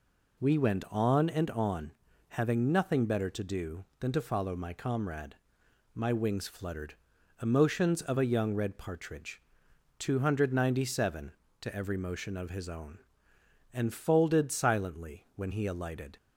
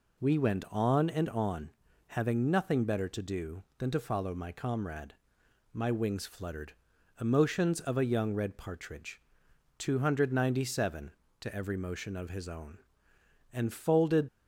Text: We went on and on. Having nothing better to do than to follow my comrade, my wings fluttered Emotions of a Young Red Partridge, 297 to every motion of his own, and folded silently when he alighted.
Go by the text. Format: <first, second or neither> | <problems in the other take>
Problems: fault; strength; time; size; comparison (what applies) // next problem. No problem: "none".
first | pauses between "fluttered" and "Emotions"; noticeable; at 6.7 s; 0.46 s long; noticeable in the first // stops before "silently when he alighted"; at 14.2 s